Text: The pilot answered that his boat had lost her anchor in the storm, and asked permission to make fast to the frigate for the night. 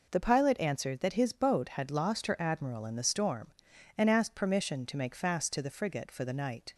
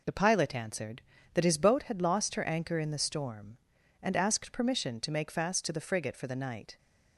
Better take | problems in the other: second | says "admiral" for "anchor"; at 2.3 s

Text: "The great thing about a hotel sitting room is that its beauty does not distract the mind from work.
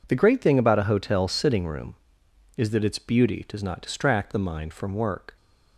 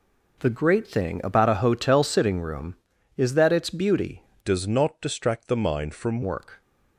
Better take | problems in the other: first | changes voice from "does" to "from"; from 4.4 to 6.2 s; 1.8 s long

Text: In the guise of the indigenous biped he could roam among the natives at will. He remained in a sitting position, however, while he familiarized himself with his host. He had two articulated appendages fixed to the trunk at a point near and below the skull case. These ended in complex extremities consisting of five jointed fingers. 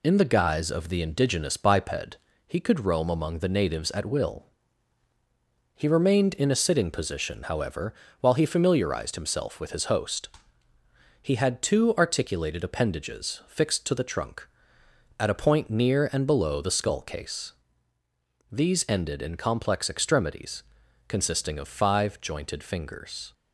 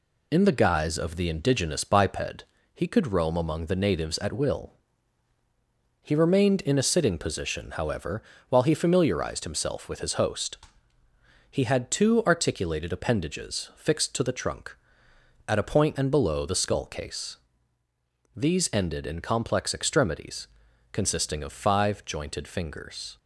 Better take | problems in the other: first | pauses between "biped" and "he"; slight; at 2.4 s; 0.28 s long; slight in the first // skips "near"; at 15.9 s // pauses between "extremities" and "consisting"; noticeable; at 20.4 s; 0.46 s long; noticeable in the first

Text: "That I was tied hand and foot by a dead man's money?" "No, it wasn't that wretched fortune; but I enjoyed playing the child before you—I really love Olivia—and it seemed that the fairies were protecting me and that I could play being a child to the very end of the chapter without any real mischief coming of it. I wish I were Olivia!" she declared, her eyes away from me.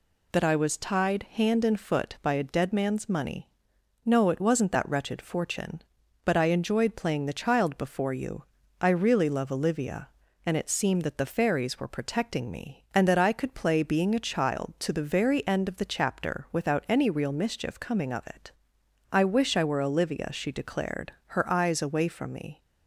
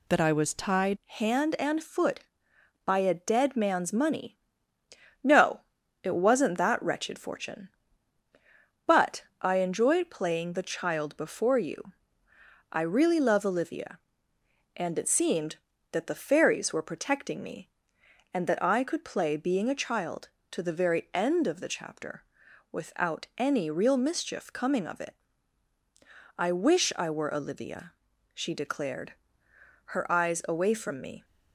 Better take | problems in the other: first | changes voice at "hand"; from 1.0 s on; 30.2 s long // pauses between "but" and "I"; slight; at 9.2 s; 0.18 s long // pauses between "chapter" and "without"; noticeable; at 22.2 s; 0.48 s long

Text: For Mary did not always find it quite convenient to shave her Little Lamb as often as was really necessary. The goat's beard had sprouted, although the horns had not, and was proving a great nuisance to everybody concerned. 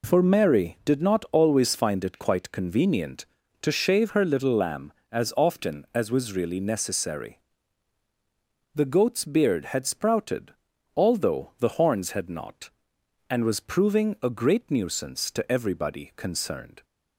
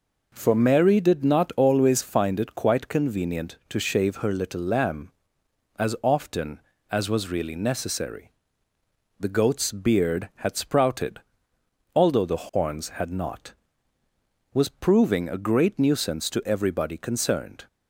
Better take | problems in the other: first | skips "and"; at 14.0 s

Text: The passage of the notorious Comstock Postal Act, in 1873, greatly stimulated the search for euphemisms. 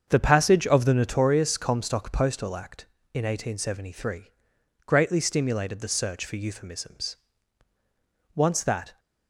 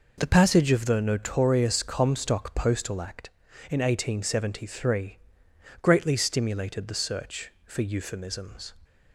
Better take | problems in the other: second | starts louder than the rest; until 1.0 s; 7 dB // goes on to say "Once that"; noticeable; from 8.3 s on; 0.64 s long

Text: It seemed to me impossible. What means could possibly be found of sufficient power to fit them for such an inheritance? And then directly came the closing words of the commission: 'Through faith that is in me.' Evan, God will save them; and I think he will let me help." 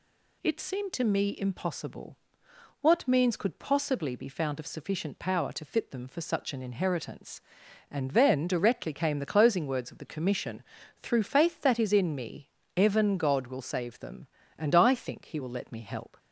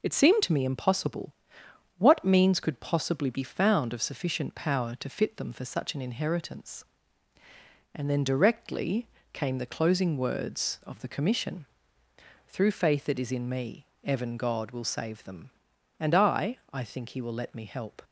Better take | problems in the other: first | pauses between "directly" and "came"; slight; at 9.0 s; 0.24 s long // says "I" twice; at 16.7 s

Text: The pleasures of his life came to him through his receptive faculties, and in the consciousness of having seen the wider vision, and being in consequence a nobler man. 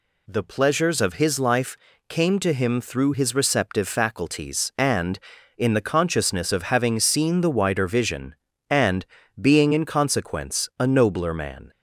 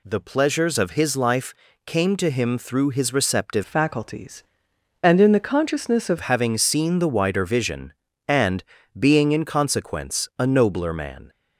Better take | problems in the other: first | pauses between "life" and "came"; slight; at 1.5 s; 0.32 s long; slight in the first // changes voice from "faculties" to "of"; from 3.6 to 6.1 s; 2.5 s long // pauses between "and" and "being"; slight; at 8.6 s; 0.36 s long; slight in the first

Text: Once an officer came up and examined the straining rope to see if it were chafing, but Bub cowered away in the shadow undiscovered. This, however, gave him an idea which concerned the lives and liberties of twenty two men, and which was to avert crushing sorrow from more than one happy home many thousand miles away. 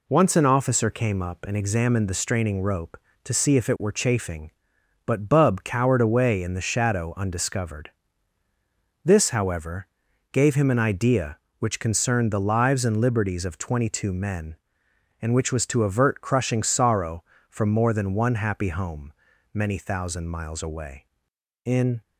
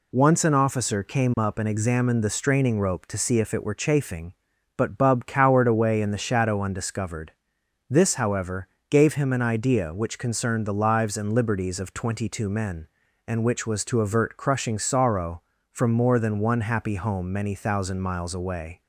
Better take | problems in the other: second | pauses between "home" and "many"; at 19.1 s; 0.40 s long // goes on to say "In"; slight; from 21.6 s on; 0.36 s long

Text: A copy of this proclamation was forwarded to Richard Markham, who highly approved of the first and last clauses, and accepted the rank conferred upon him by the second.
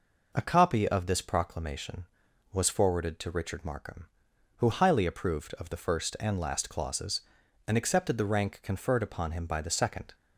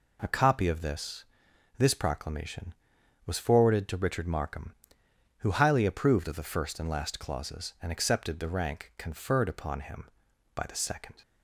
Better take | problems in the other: first | says "this" twice; at 1.7 s

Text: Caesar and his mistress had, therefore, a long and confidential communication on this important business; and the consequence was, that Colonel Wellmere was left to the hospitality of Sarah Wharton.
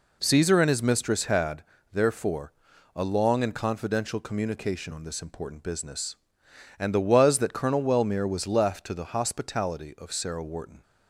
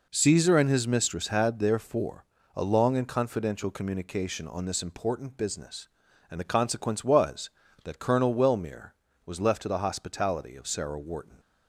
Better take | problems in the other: second | skips "consequence"; at 6.9 s

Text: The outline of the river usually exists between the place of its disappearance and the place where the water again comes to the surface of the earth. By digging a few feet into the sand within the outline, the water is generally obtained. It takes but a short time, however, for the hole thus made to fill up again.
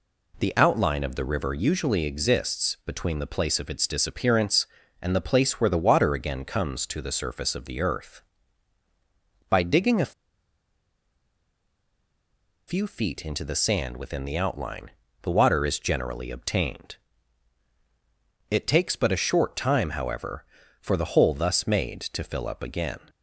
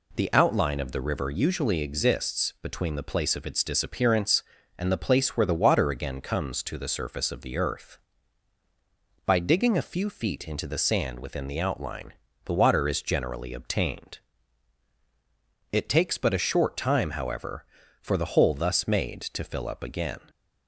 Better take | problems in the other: second | pauses between "a" and "few"; strong; at 10.1 s; 2.5 s long

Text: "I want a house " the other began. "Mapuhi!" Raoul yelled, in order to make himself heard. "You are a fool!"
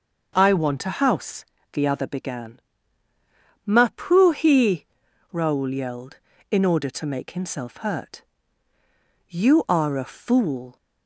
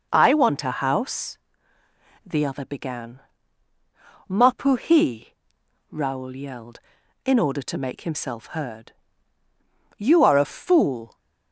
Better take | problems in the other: second | says "hurt" for "heard"; at 7.7 s

